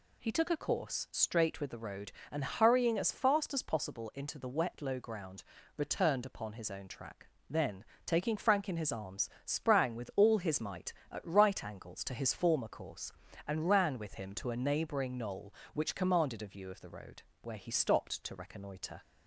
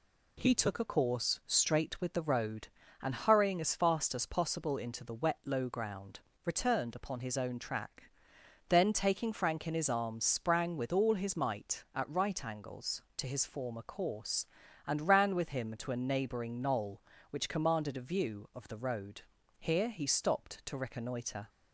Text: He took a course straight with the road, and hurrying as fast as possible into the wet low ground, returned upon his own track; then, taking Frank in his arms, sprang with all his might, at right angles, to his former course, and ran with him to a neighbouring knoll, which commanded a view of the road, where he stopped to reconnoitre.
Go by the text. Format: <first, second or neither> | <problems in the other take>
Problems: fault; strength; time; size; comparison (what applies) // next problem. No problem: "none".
first | says "here" for "where"; at 19.5 s